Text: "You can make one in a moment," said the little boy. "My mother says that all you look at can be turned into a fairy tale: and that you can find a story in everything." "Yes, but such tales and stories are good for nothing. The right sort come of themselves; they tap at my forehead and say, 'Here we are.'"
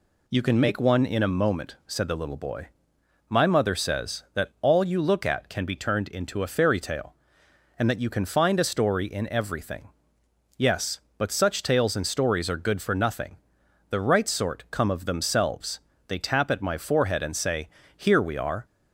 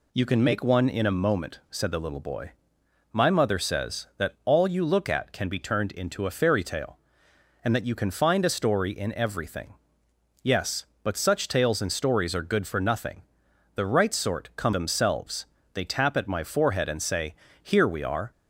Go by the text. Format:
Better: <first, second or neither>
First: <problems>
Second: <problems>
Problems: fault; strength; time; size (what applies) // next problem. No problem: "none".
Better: first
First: none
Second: skips "of"; at 14.7 s